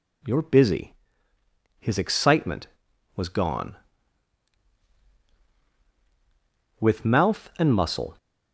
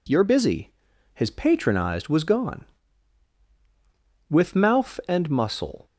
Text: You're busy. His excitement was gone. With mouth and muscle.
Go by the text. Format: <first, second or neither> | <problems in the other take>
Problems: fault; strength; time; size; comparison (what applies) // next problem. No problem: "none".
first | says "patronized" for "excitement"; at 1.2 s